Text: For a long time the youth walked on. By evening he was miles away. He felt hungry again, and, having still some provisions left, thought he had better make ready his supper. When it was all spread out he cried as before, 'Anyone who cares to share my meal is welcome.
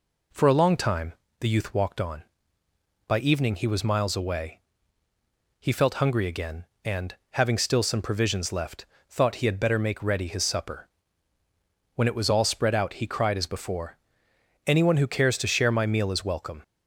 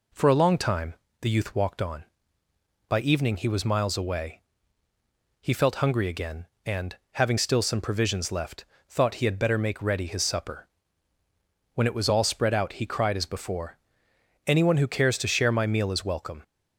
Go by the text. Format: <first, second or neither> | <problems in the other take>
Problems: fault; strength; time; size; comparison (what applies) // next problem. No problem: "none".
neither | pauses between "time" and "the"; slight; the same in both